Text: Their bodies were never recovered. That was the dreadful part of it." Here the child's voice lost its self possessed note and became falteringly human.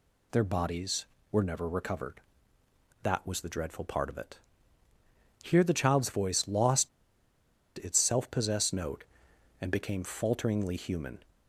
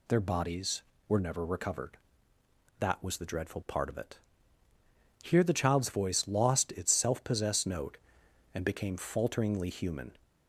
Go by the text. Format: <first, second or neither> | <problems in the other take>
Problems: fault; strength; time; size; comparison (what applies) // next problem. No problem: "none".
second | pauses between "lost" and "its"; noticeable; at 6.8 s; 0.88 s long